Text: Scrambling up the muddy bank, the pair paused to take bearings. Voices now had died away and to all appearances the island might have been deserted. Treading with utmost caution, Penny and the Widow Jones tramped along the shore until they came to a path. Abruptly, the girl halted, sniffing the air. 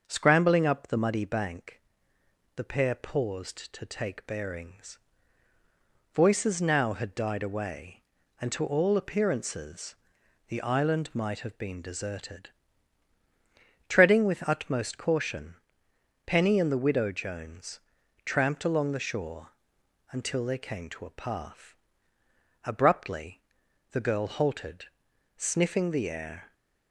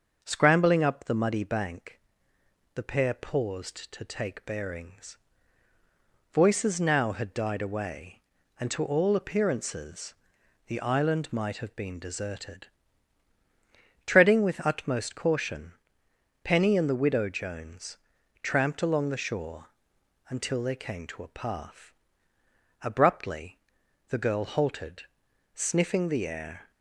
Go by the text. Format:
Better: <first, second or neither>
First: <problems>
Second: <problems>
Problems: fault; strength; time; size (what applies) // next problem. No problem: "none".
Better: neither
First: starts louder than the rest; until 1.0 s; 6 dB // pauses between "appearances" and "the"; noticeable; at 9.9 s; 0.54 s long // pauses between "Jones" and "tramped"; noticeable; at 17.7 s; 0.46 s long // pauses between "shore" and "until"; noticeable; at 19.5 s; 0.60 s long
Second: starts louder than the rest; until 1.2 s; 6 dB // pauses between "appearances" and "the"; noticeable; at 10.1 s; 0.54 s long // pauses between "Jones" and "tramped"; noticeable; at 17.9 s; 0.46 s long // pauses between "shore" and "until"; noticeable; at 19.6 s; 0.60 s long